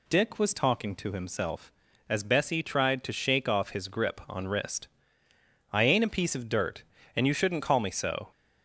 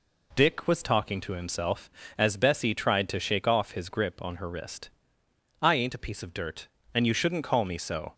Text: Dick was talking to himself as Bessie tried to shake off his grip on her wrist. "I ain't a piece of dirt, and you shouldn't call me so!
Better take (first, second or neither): second